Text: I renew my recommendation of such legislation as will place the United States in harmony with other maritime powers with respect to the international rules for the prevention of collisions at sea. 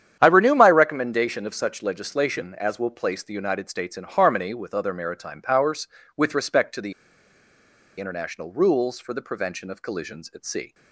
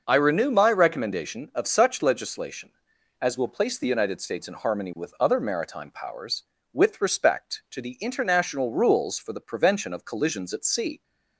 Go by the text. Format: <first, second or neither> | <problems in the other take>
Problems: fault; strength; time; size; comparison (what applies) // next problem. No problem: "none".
second | starts louder than the rest; strong; until 1.2 s; 9.5 dB // pauses between "the" and "international"; at 6.9 s; 1.0 s long